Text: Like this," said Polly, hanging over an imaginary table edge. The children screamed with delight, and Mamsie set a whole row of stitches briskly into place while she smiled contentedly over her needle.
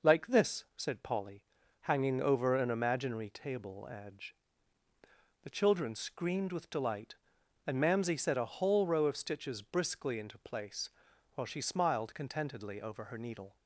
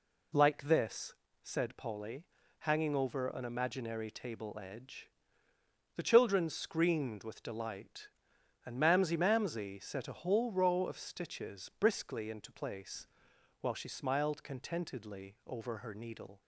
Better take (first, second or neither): first